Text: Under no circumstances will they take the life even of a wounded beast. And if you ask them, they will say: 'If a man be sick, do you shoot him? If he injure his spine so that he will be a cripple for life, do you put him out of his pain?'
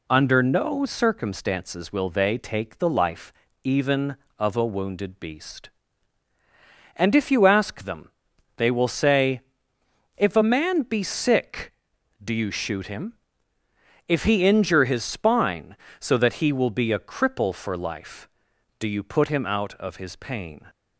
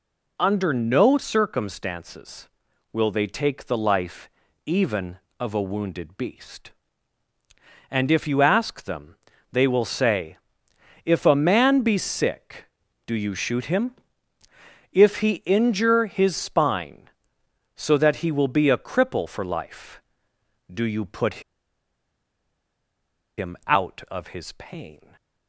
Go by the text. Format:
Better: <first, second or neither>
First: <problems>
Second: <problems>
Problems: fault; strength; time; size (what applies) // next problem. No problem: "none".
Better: first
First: pauses between "life" and "even"; slight; at 3.3 s; 0.32 s long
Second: pauses between "life" and "even"; at 4.2 s; 0.38 s long // pauses between "put" and "him"; strong; at 21.4 s; 1.9 s long // stays silent after the last word; slight; from 24.9 s on; 0.5 s long